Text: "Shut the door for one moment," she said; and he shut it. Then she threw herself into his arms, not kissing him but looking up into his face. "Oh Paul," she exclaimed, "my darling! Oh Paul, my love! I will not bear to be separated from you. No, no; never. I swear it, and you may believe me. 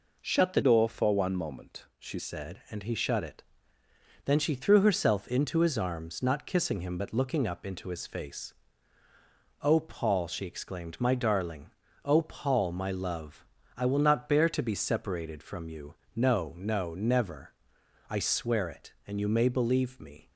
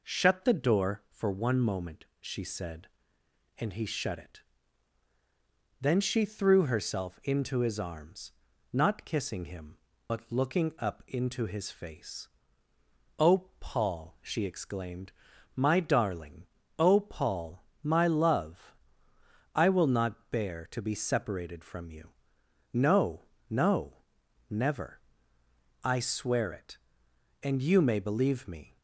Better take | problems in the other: second | changes voice from "door" to "she"; from 0.6 to 2.1 s; 1.5 s long

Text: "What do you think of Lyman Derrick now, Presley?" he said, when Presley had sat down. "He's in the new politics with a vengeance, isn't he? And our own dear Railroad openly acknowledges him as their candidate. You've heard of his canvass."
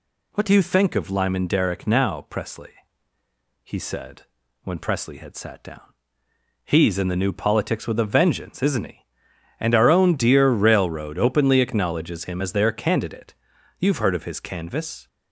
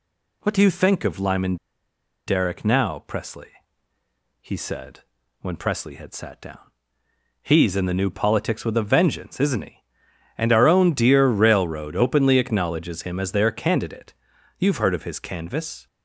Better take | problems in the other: first | pauses between "Lyman" and "Derrick"; noticeable; at 1.5 s; 0.71 s long

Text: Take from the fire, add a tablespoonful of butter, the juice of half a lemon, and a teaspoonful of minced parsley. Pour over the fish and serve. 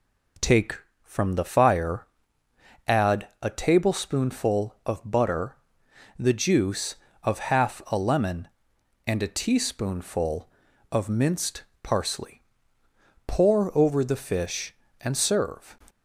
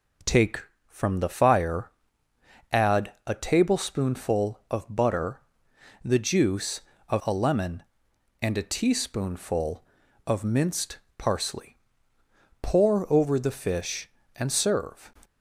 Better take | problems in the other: first | skips "half"; at 7.2 s // pauses between "minced" and "parsley"; slight; at 10.9 s; 0.18 s long; slight in the first

